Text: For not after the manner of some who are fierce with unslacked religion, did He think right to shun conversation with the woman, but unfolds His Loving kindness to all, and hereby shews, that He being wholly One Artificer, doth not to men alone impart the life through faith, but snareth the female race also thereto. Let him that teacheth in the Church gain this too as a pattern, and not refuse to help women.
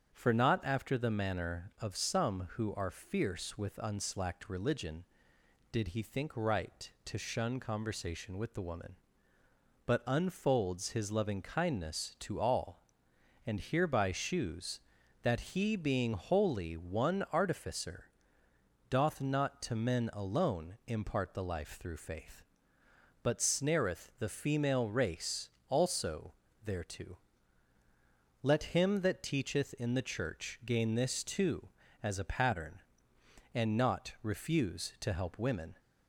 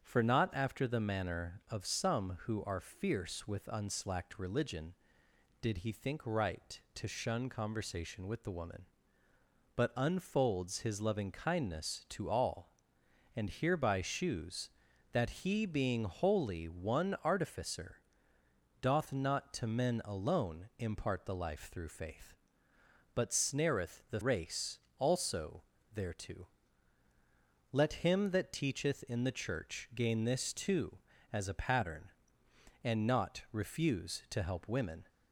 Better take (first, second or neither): first